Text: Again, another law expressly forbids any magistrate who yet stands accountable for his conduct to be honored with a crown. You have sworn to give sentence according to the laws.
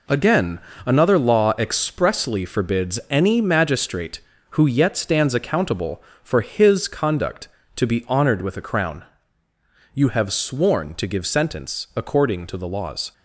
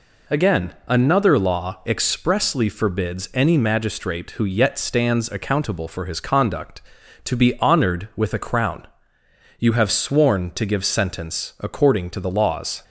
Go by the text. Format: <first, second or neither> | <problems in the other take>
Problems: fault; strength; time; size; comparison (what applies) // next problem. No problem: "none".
neither | none